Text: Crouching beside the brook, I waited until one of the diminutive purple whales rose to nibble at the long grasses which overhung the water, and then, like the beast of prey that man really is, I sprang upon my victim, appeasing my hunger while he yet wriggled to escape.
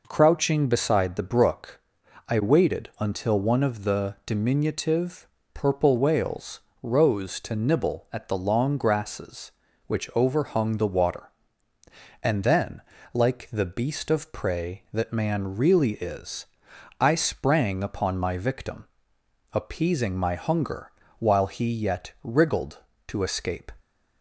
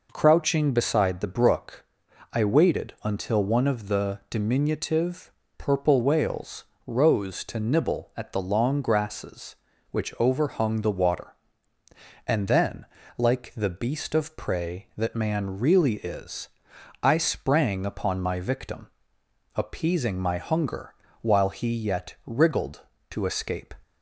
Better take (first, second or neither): neither